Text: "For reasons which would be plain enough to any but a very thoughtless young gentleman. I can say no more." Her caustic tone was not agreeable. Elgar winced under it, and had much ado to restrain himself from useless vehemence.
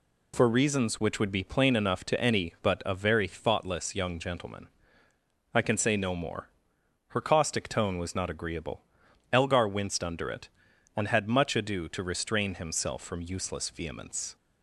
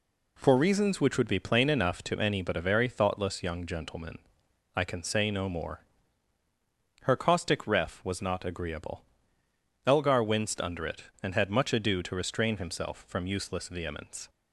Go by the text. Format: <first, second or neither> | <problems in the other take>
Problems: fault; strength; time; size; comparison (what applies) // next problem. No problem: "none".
first | says "ref" for "tone"; at 7.6 s